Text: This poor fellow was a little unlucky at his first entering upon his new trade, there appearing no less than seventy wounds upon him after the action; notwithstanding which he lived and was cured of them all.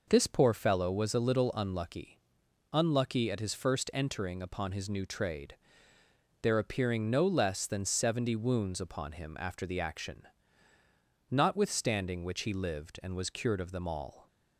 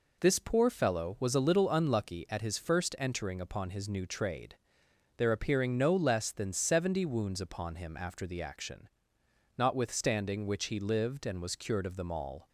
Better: second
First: says "unlucky" twice; at 2.7 s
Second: none

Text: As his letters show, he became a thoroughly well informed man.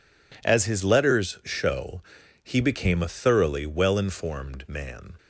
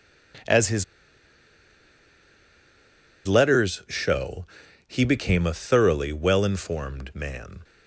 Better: first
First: none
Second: pauses between "his" and "letters"; strong; at 0.8 s; 2.4 s long

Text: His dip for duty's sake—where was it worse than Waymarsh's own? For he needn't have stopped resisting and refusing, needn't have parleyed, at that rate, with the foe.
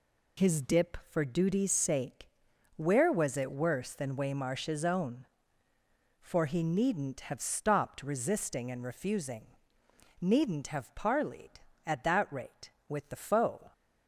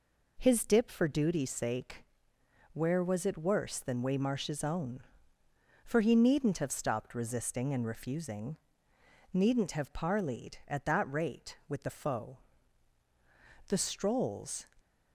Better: first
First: none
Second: goes on to say "The strolls"; noticeable; from 13.6 s on; 1.0 s long

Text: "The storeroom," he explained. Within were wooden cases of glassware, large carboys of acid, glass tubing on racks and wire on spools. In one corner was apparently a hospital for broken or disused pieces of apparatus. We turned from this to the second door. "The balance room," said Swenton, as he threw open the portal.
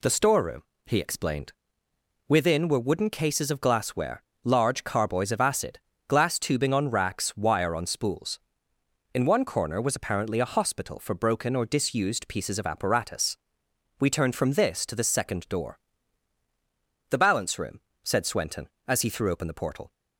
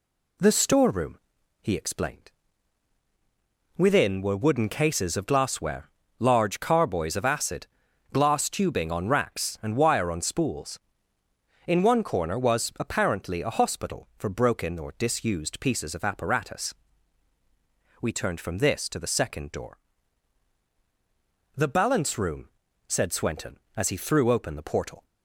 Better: second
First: skips "and"; at 7.3 s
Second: none

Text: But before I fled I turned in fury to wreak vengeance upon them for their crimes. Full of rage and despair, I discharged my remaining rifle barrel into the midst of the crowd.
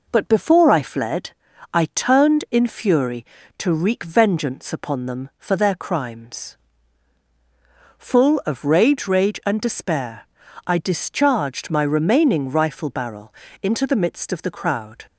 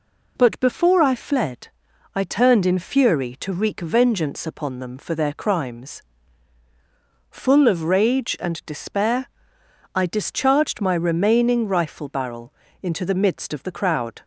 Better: second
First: pauses between "fled" and "I"; at 1.3 s; 0.42 s long // says "rage" twice; at 9.0 s // pauses between "barrel" and "into"; slight; at 13.3 s; 0.28 s long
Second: pauses between "fled" and "I"; noticeable; at 1.6 s; 0.46 s long // pauses between "barrel" and "into"; slight; at 12.5 s; 0.28 s long

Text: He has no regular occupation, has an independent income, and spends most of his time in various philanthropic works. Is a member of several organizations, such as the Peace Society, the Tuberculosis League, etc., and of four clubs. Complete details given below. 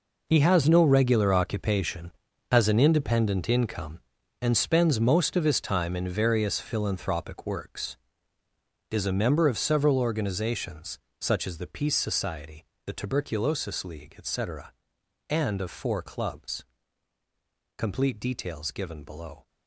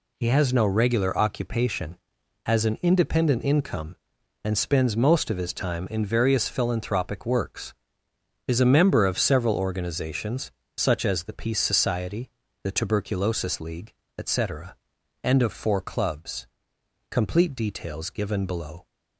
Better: second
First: gets quieter; strong; throughout; 13 dB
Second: none

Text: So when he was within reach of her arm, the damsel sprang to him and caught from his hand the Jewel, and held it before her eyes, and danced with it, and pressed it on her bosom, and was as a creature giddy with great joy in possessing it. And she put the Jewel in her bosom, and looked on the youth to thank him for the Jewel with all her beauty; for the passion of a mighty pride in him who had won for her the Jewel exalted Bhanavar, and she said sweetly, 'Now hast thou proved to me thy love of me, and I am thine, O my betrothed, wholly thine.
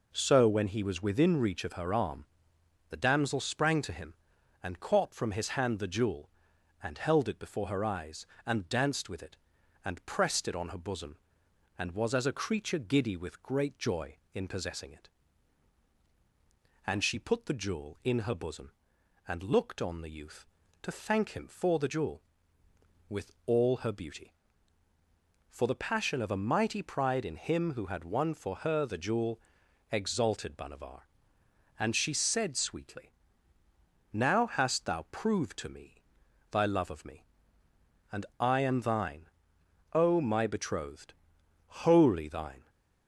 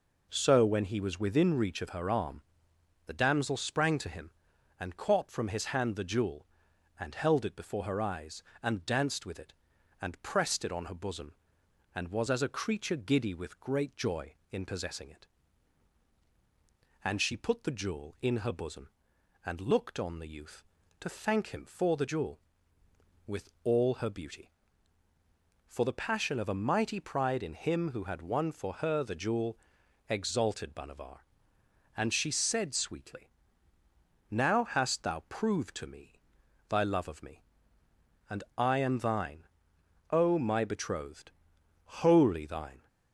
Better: neither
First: pauses between "Jewel" and "exalted"; noticeable; at 29.3 s; 0.52 s long // pauses between "me" and "thy"; noticeable; at 35.9 s; 0.56 s long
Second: pauses between "Jewel" and "exalted"; noticeable; at 29.5 s; 0.52 s long // pauses between "me" and "thy"; noticeable; at 36.1 s; 0.56 s long

